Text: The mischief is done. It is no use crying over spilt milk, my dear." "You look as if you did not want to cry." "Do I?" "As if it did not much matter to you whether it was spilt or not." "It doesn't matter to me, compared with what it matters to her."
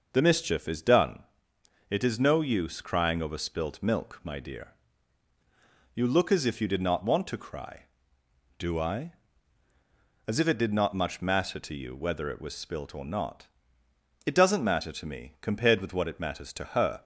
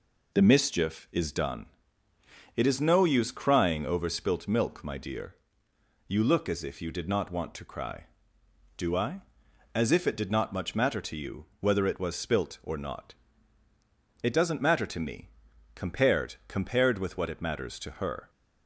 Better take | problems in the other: first | says "compared" twice; at 16.4 s

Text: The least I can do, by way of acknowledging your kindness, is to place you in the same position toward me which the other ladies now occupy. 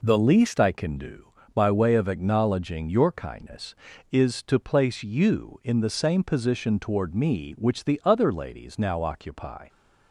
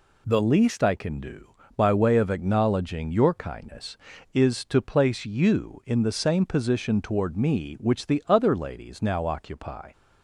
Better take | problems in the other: second | starts louder than the rest; noticeable; until 1.1 s; 4 dB

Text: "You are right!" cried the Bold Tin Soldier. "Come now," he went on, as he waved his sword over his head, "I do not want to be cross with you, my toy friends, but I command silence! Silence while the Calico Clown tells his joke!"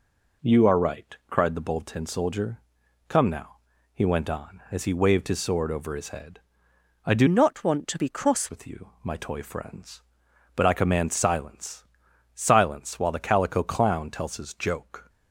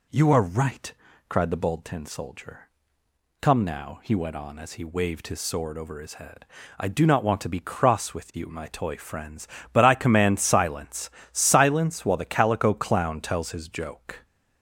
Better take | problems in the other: second | changes voice from "not" to "cross"; from 7.2 to 8.4 s; 1.2 s long

